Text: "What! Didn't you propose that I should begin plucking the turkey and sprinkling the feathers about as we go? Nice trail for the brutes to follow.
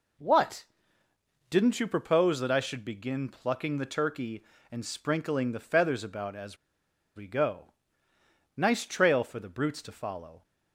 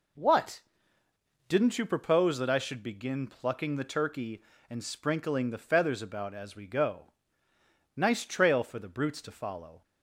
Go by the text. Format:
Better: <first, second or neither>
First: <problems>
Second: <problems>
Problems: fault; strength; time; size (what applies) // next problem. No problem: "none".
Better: second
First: pauses between "as" and "we"; noticeable; at 6.5 s; 0.59 s long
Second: none